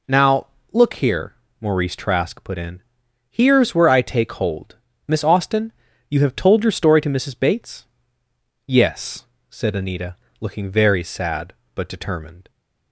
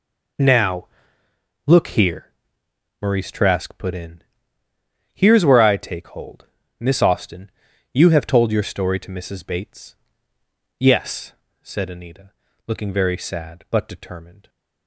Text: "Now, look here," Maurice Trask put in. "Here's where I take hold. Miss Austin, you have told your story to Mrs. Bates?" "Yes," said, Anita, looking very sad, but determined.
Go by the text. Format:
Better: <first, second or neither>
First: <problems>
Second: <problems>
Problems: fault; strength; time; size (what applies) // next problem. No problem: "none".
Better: neither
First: none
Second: none